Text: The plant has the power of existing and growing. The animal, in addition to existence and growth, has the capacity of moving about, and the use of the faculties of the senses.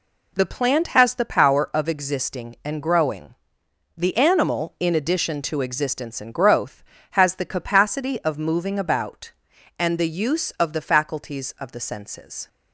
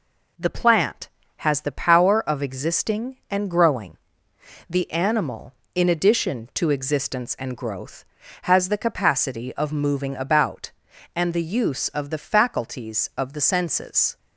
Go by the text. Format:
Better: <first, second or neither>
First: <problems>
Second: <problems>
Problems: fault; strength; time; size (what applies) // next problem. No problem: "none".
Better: neither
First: none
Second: none